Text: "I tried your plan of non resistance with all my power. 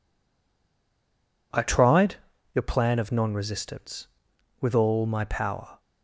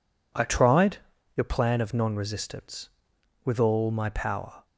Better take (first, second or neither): second